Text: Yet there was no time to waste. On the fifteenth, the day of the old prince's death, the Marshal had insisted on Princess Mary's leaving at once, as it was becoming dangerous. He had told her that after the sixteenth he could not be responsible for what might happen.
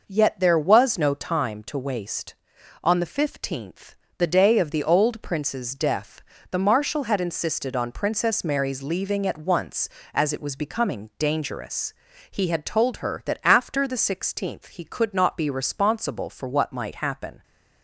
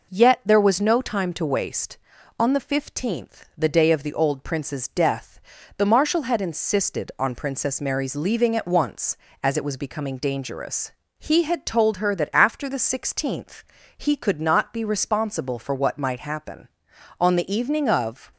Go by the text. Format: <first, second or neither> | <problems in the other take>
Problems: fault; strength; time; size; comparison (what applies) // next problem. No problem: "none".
first | pauses between "sixteenth" and "he"; slight; at 13.6 s; 0.34 s long // goes on to say "On the evening of"; noticeable; from 17.1 s on; 1.1 s long